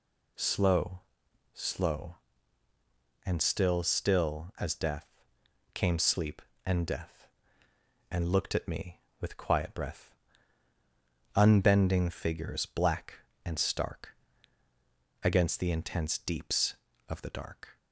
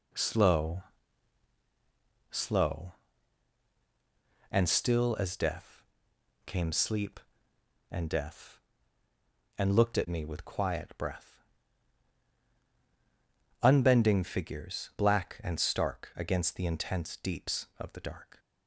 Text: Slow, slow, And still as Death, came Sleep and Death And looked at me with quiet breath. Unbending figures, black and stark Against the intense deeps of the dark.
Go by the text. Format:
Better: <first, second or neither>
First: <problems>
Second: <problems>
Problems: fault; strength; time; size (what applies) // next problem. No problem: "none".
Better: second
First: says "still" twice; at 3.8 s // pauses between "stark" and "Against"; at 14.1 s; 1.0 s long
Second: none